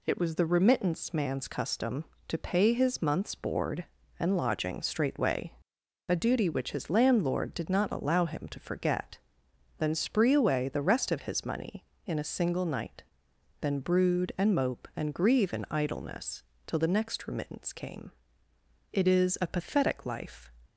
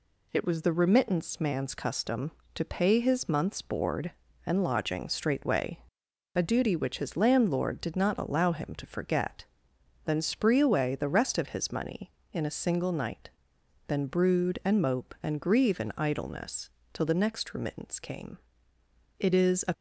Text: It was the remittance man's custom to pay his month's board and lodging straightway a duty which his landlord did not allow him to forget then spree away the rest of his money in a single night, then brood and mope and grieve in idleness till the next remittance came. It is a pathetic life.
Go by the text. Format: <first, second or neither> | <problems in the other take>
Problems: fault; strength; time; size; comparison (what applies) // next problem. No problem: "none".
first | pauses between "straightway" and "a"; noticeable; at 5.7 s; 0.56 s long; noticeable in the first // pauses between "forget" and "then"; noticeable; at 9.4 s; 0.60 s long; noticeable in the first // pauses between "idleness" and "till"; slight; at 16.6 s; 0.24 s long; slight in the first // stops before "pathetic life"; at 19.7 s